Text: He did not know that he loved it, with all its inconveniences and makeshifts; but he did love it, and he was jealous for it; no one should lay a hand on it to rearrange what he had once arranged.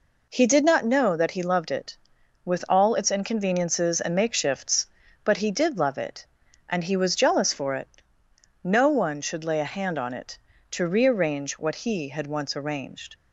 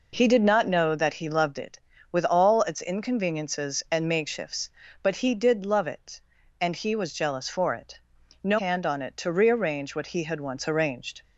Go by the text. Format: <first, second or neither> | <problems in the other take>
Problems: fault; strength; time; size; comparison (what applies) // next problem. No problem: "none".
first | skips "one should lay a"; at 8.5 s